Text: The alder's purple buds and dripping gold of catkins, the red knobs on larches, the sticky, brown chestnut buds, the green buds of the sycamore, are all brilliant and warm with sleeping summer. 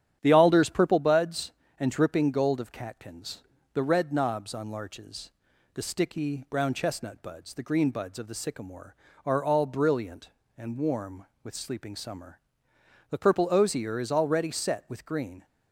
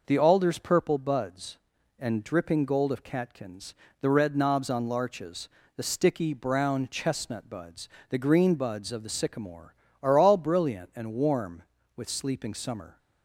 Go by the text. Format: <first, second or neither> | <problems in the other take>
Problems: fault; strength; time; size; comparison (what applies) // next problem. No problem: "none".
second | starts louder than the rest; strong; until 1.2 s; 10 dB // goes on to say "The purple osier is already set with green"; strong; from 13.1 s on; 2.3 s long